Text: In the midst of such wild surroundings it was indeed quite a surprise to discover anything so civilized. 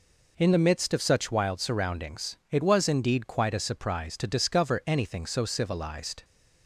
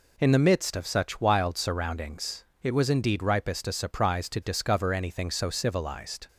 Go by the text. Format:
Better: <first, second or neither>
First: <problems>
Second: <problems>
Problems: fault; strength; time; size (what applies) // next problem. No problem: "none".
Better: first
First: none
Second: pauses between "surroundings" and "it"; slight; at 2.4 s; 0.18 s long // says "ripest" for "quite"; at 3.2 s